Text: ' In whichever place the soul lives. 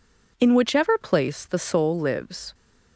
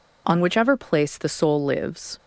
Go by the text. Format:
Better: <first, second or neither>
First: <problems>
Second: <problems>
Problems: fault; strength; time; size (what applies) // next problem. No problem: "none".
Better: first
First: none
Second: says "On" for "In"; at 0.2 s